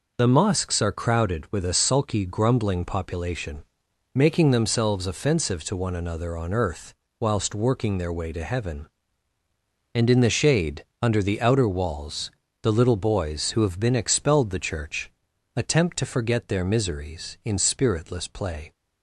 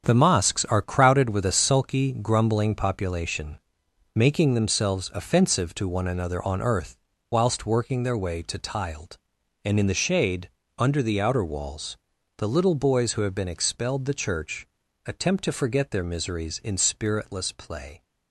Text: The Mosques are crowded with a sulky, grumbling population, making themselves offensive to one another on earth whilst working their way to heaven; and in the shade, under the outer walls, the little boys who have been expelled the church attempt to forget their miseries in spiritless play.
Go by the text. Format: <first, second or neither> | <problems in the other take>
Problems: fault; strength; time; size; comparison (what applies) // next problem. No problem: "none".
first | starts louder than the rest; until 1.0 s; 7 dB // pauses between "earth" and "whilst"; slight; at 6.9 s; 0.36 s long; slight in the first // says "tiled" for "heaven"; at 8.5 s // pauses between "church" and "attempt"; at 14.6 s; 0.40 s long; noticeable in the first